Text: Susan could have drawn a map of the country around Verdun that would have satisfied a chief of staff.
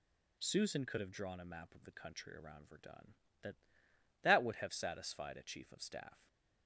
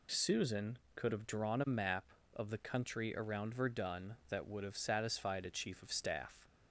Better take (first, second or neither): second